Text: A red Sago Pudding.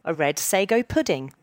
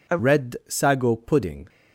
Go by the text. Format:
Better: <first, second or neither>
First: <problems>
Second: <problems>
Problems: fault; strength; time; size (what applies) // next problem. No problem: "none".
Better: first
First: none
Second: changes voice at "red"; from 0.1 s on; 1.5 s long